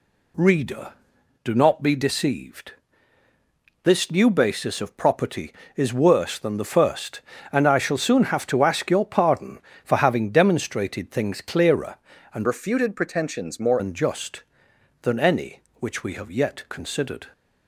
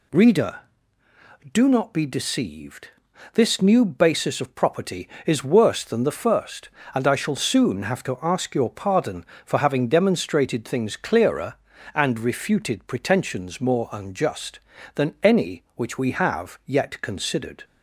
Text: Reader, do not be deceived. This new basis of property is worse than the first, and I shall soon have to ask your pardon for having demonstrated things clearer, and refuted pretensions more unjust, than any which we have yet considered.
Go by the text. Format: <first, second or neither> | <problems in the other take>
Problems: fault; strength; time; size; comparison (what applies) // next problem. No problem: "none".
second | changes voice from "refuted" to "more"; from 12.4 to 13.8 s; 1.4 s long